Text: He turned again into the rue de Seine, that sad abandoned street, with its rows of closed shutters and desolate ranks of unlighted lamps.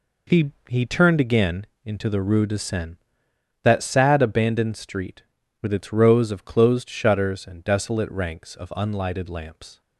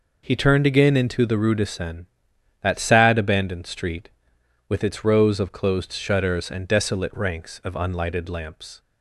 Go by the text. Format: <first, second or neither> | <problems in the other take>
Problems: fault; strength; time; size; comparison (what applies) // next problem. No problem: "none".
second | says "He" twice; at 0.6 s // pauses between "again" and "into"; slight; at 1.6 s; 0.22 s long